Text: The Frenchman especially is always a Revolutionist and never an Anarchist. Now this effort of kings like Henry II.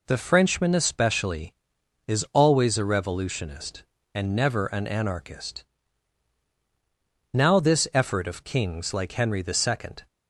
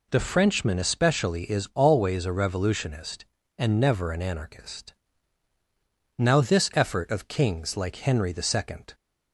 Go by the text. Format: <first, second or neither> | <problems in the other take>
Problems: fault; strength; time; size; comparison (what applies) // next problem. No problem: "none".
neither | none